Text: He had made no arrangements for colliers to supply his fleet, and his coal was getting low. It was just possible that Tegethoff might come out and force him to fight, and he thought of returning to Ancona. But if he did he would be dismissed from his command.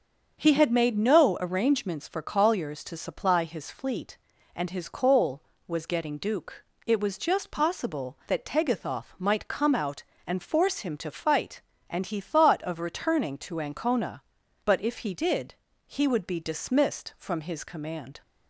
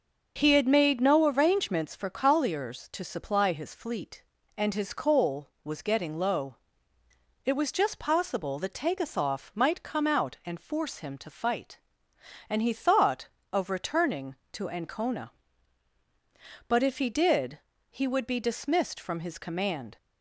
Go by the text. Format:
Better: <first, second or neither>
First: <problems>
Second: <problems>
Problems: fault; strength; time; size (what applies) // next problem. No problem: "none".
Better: second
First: starts louder than the rest; until 1.4 s; 6.5 dB // says "duke" for "low"; at 6.1 s // pauses between "did" and "he"; slight; at 15.5 s; 0.30 s long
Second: pauses between "did" and "he"; slight; at 17.5 s; 0.32 s long